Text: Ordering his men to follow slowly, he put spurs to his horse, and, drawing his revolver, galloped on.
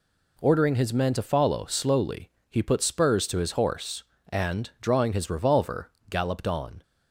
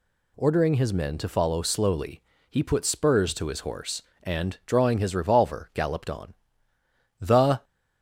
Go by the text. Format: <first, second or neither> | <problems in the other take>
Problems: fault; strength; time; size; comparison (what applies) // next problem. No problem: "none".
first | goes on to say "The"; slight; from 7.1 s on; 0.44 s long